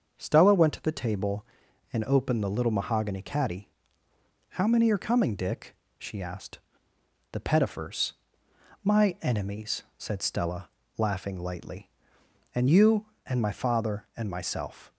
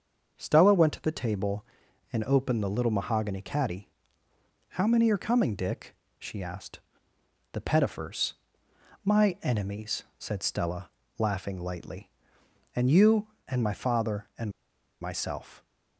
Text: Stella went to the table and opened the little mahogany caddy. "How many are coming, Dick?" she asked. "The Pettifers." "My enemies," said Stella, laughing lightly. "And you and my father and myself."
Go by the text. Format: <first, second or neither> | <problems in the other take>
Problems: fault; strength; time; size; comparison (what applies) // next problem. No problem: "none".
first | starts louder than the rest; until 1.4 s; 6.5 dB; also in the first // pauses between "and" and "myself"; noticeable; at 14.5 s; 0.50 s long